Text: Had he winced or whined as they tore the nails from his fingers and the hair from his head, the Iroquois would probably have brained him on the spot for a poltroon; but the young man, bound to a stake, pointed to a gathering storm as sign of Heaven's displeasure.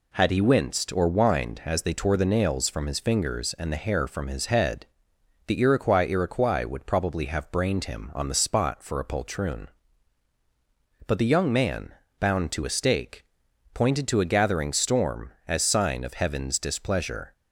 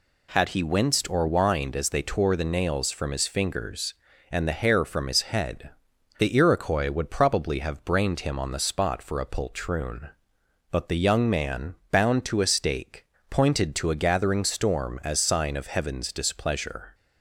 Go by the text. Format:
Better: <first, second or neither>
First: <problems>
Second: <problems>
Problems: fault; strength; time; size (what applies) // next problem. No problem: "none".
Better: second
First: says "Iroquois" twice; at 6.0 s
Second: none